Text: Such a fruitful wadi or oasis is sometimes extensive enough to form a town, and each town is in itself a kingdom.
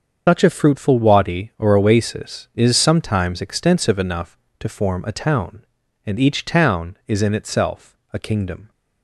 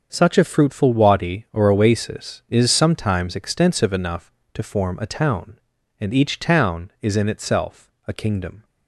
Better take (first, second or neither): second